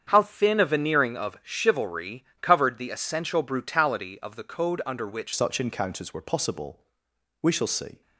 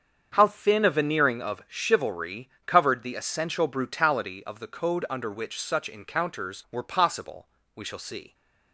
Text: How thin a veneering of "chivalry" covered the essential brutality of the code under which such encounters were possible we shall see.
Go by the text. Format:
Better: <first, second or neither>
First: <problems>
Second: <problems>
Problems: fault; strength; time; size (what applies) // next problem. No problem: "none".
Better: second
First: starts louder than the rest; strong; until 1.0 s; 7.5 dB // pauses between "chivalry" and "covered"; slight; at 2.2 s; 0.16 s long // changes voice at "such"; from 5.3 s on; 2.7 s long // pauses between "possible" and "we"; noticeable; at 6.8 s; 0.58 s long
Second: starts louder than the rest; until 1.3 s; 7 dB // pauses between "chivalry" and "covered"; slight; at 2.4 s; 0.16 s long // pauses between "possible" and "we"; slight; at 7.4 s; 0.28 s long